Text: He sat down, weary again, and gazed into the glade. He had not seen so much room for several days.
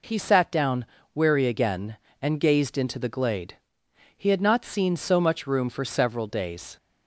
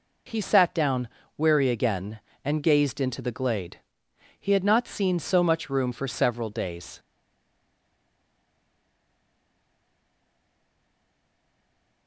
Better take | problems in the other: first | stays silent after the last word; strong; from 6.9 s on; 5.1 s long

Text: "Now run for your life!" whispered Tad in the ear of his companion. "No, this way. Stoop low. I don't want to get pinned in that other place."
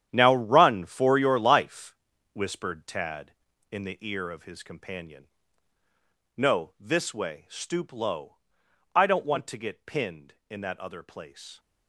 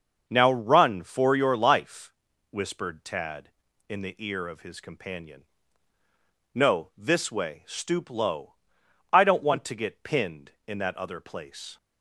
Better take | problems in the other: second | gets quieter; strong; throughout; 12.5 dB // starts louder than the rest; strong; until 1.1 s; 10 dB; also in the second

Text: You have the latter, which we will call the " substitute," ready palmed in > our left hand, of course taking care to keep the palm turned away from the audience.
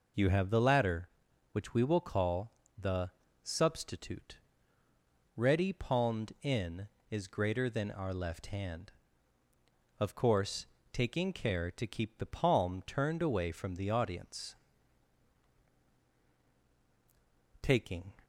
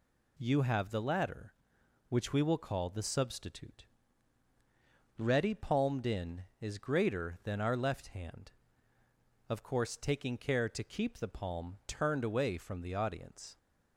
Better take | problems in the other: second | pauses between "call" and "the"; slight; at 2.5 s; 0.24 s long // pauses between "course" and "taking"; slight; at 10.6 s; 0.26 s long // goes on to say "Taking"; from 17.6 s on; 0.54 s long

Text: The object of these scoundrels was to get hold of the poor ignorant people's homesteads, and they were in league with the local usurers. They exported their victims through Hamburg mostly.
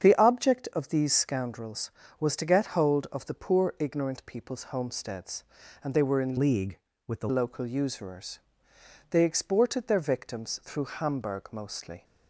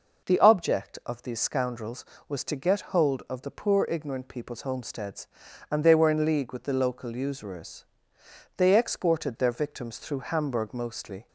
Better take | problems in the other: second | starts louder than the rest; strong; until 1.0 s; 8 dB // changes voice from "league" to "the"; from 6.3 to 7.2 s; 0.9 s long

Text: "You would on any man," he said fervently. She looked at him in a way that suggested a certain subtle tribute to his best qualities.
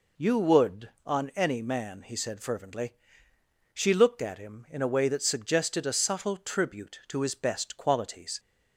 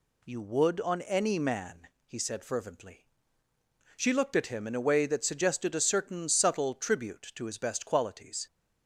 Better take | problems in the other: second | skips "certain"; at 5.9 s

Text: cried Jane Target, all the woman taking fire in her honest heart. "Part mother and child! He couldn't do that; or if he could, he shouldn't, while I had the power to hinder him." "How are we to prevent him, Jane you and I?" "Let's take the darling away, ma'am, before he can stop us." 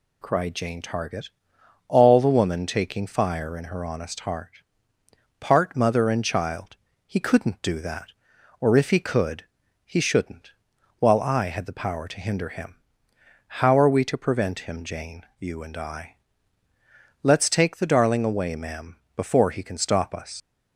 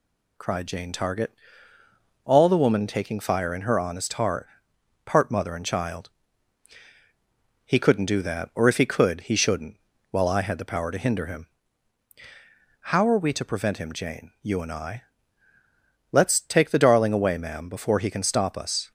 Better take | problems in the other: second | leaves "us" unfinished; at 20.4 s; 85 ms

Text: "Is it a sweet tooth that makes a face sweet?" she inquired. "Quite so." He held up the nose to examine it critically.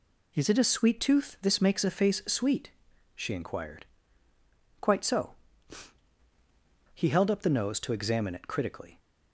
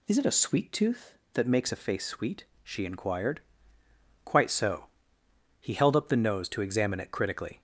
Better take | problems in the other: second | says "this" for "that"; at 1.4 s

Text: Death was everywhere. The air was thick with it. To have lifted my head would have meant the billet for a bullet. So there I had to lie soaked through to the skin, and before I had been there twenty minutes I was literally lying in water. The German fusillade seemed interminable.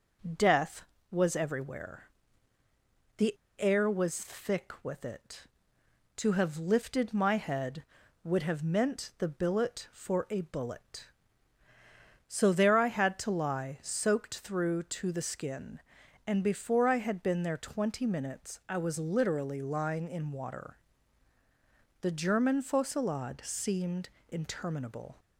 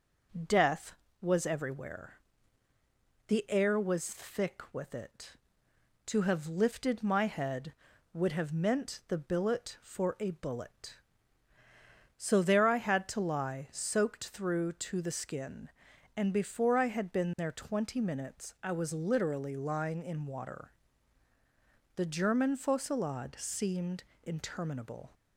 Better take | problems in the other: second | pauses between "The" and "air"; slight; at 3.3 s; 0.24 s long // pauses between "seemed" and "interminable"; slight; at 24.0 s; 0.20 s long; slight in the second

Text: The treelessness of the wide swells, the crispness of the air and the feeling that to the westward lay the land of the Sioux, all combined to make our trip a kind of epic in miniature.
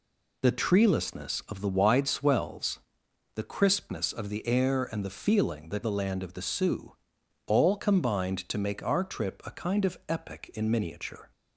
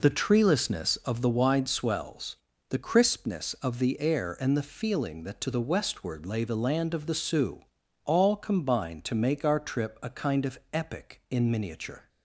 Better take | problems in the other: second | skips "to the westward lay"; at 5.8 s

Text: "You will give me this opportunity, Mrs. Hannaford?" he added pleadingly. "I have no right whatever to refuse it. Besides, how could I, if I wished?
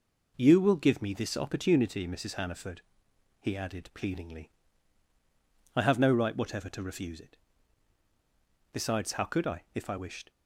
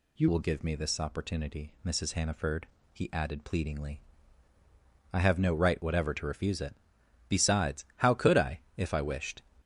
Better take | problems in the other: first | changes voice at "will"; from 0.2 s on; 9.2 s long

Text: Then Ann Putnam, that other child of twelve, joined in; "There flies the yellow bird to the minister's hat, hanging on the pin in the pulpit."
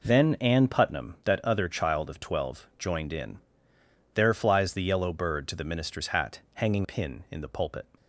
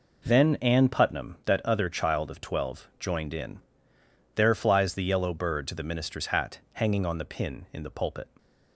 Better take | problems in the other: second | skips "on the"; at 6.8 s

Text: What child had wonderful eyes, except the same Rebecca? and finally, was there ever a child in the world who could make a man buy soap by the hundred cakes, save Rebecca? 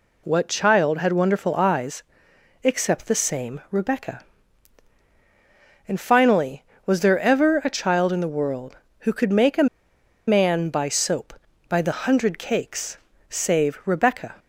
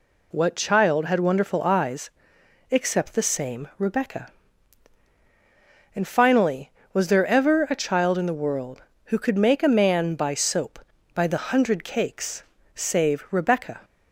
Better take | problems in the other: second | pauses between "a" and "man"; noticeable; at 9.6 s; 0.61 s long

